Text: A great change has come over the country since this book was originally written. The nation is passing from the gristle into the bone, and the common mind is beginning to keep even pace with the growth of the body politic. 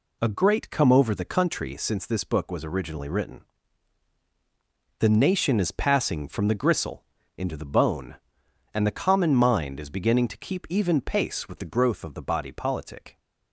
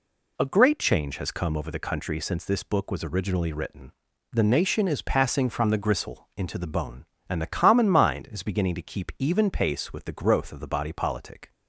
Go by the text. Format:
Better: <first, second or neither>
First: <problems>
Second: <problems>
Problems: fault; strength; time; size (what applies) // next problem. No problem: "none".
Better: second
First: skips "change has"; at 0.6 s // pauses between "gristle" and "into"; slight; at 7.0 s; 0.32 s long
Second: none